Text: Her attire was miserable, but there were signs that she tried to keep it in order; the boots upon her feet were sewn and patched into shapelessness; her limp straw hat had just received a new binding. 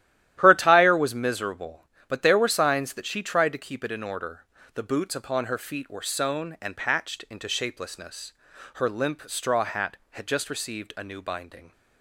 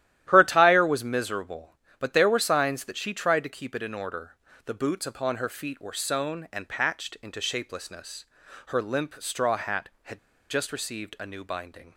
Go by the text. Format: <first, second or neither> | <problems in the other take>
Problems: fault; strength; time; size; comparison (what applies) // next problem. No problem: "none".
first | starts louder than the rest; strong; until 1.2 s; 13 dB; strong in the first // pauses between "had" and "just"; slight; at 10.1 s; 0.30 s long